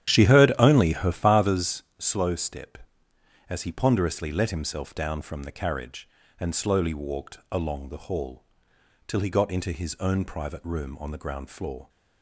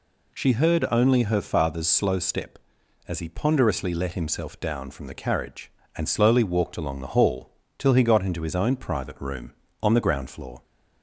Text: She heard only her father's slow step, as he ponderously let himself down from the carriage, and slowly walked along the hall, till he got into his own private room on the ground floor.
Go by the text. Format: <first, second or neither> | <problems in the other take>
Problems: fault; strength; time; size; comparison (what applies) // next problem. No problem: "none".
second | starts louder than the rest; strong; until 1.8 s; 11 dB // pauses between "father's" and "slow"; slight; at 1.8 s; 0.16 s long